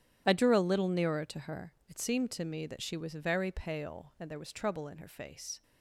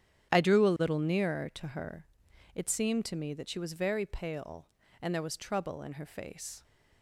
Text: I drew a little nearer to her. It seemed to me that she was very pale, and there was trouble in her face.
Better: neither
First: starts louder than the rest; strong; until 1.2 s; 11 dB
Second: starts louder than the rest; strong; until 1.3 s; 10 dB

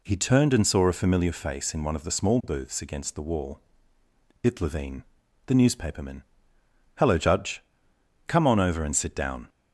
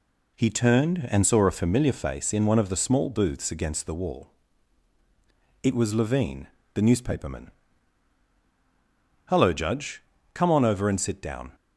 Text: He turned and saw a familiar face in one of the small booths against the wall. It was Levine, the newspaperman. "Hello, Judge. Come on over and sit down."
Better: second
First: skips "was"; at 4.6 s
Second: none

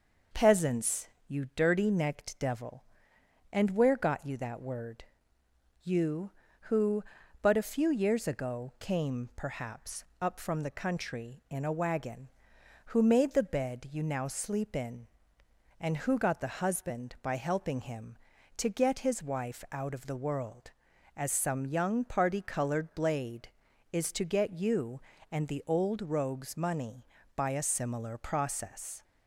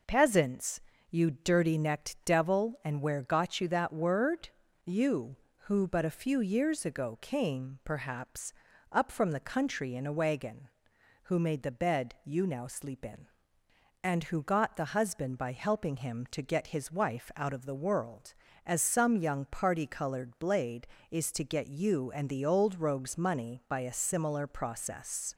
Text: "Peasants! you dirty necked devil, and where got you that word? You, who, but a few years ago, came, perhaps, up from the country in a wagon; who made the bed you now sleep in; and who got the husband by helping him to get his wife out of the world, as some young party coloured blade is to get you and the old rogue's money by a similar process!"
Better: neither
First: none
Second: none

